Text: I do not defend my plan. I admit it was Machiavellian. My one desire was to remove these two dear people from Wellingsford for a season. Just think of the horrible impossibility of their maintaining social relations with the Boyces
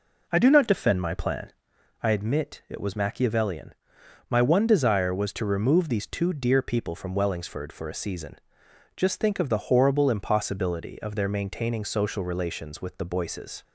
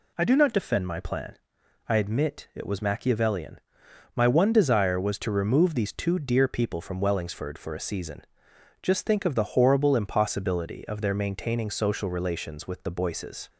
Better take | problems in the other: second | starts louder than the rest; noticeable; until 2.0 s; 4.5 dB

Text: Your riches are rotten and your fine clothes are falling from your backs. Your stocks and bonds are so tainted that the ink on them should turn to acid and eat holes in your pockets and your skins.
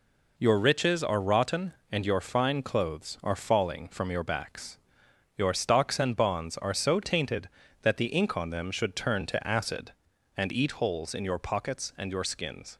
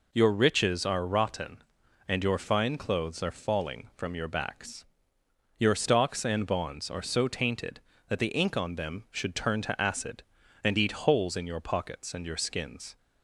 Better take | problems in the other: neither | none

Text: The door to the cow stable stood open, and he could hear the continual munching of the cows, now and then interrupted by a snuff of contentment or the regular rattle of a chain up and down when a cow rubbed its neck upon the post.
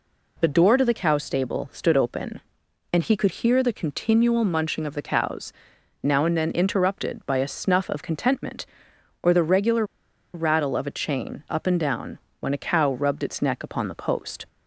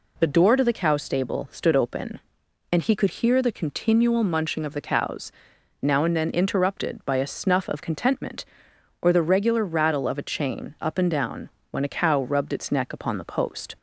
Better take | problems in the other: second | pauses between "regular" and "rattle"; noticeable; at 9.8 s; 0.50 s long // pauses between "down" and "when"; slight; at 12.1 s; 0.20 s long; slight in the second

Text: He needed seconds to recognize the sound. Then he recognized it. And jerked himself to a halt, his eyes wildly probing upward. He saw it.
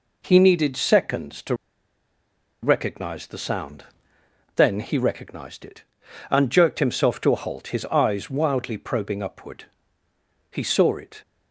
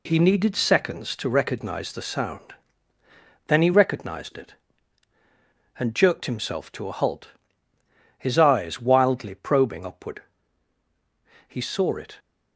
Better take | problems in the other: second | pauses between "to" and "recognize"; at 1.5 s; 1.0 s long

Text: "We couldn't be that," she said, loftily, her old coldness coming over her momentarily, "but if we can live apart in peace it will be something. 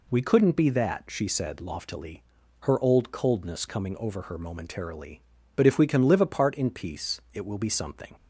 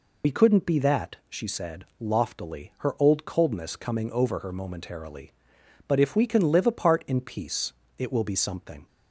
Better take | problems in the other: first | loses the start of "We"; at 0.2 s; 45 ms // pauses between "peace" and "it"; slight; at 7.7 s; 0.26 s long

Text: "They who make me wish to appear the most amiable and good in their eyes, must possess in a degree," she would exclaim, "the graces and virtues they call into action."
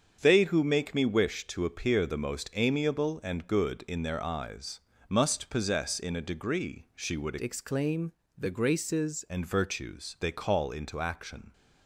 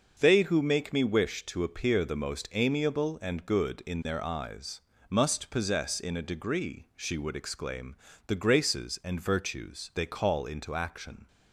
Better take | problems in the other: second | starts louder than the rest; strong; until 1.2 s; 7 dB; noticeable in the second // changes voice from "exclaim" to "graces"; from 7.4 to 9.2 s; 1.8 s long

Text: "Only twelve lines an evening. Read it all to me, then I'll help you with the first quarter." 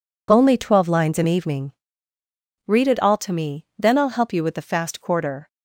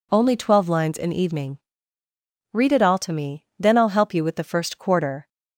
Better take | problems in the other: second | says "fast" for "first"; at 4.6 s

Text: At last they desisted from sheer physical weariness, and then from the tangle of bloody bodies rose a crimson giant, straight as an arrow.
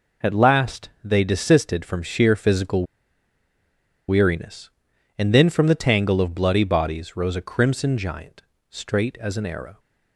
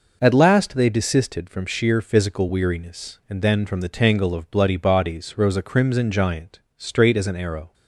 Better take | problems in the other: second | pauses between "last" and "they"; slight; at 0.8 s; 0.16 s long // pauses between "physical" and "weariness"; at 2.8 s; 1.2 s long

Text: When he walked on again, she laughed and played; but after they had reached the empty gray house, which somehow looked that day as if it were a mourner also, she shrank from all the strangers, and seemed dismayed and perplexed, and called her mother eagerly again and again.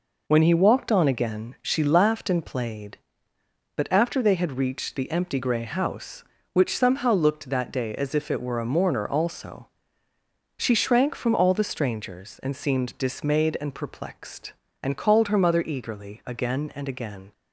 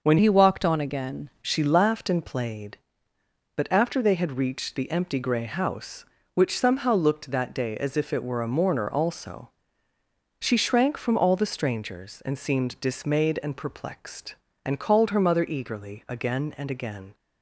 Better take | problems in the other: first | changes voice from "he" to "again"; from 0.1 to 1.2 s; 1.1 s long

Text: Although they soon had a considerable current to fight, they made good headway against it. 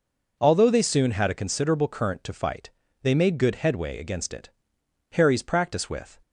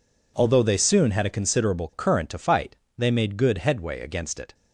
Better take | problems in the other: second | goes on to say "Harry's practice with"; noticeable; from 5.1 s on; 1.0 s long

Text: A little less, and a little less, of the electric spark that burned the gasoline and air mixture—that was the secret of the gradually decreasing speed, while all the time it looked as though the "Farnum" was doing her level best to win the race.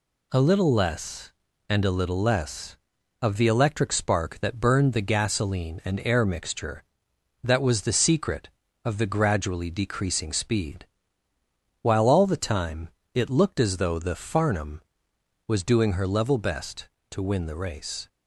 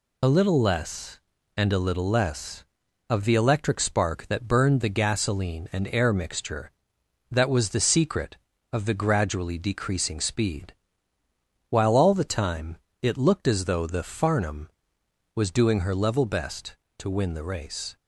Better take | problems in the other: first | loses the start of "A"; at 0.2 s; 30 ms // pauses between "time" and "it"; slight; at 12.7 s; 0.26 s long; slight in the first

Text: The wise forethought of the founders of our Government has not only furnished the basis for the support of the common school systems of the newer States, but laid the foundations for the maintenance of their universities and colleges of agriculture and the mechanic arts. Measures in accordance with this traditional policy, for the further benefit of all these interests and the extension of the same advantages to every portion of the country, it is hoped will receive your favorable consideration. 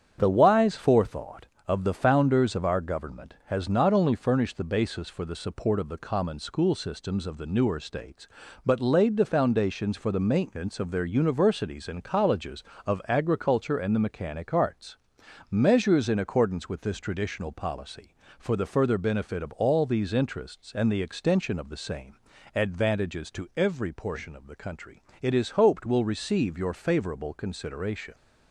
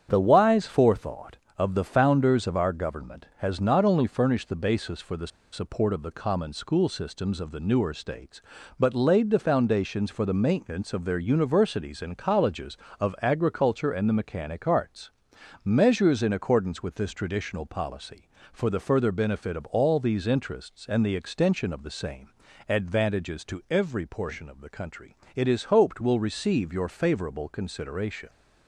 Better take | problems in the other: first | starts louder than the rest; strong; until 1.1 s; 8.5 dB; strong in the first // pauses between "the" and "support"; slight; at 5.2 s; 0.24 s long // pauses between "same" and "advantages"; at 22.2 s; 0.40 s long; also in the first

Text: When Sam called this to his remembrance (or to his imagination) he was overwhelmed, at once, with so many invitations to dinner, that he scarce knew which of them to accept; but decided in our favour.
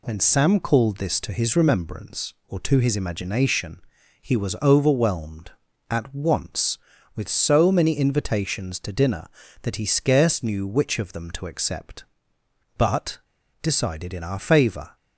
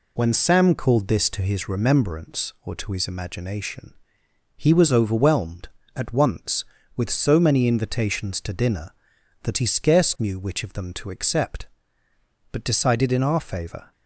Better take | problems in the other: second | pauses between "but" and "decided"; at 13.1 s; 0.44 s long

